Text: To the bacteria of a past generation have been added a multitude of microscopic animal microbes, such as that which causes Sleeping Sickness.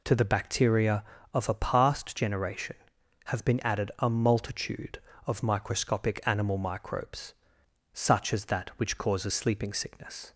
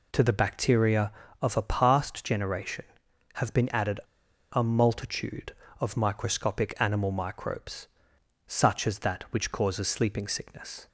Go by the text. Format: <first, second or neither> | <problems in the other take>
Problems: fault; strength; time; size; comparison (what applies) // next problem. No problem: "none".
first | pauses between "added" and "a"; noticeable; at 3.9 s; 0.52 s long